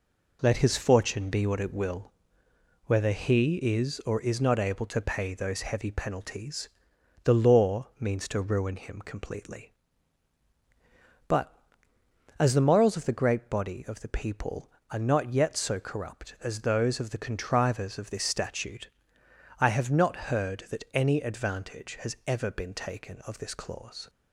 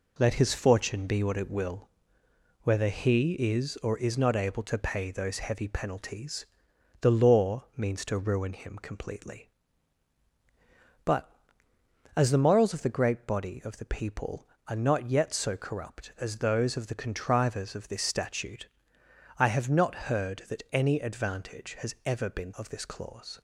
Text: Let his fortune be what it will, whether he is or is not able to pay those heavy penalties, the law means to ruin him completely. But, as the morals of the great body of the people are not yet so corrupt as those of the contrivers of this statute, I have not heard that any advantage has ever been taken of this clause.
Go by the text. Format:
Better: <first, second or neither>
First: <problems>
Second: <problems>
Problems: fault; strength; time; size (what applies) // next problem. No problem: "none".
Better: first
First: none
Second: skips "taken"; at 22.5 s